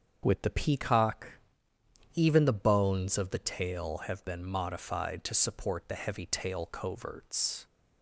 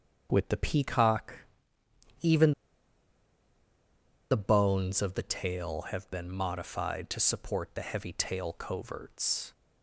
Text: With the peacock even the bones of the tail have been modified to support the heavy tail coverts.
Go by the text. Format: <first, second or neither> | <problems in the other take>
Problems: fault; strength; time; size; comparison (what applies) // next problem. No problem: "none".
first | starts louder than the rest; until 1.3 s; 7 dB; also in the first // pauses between "peacock" and "even"; noticeable; at 1.3 s; 0.82 s long; noticeable in the first // pauses between "even" and "the"; strong; at 2.5 s; 1.7 s long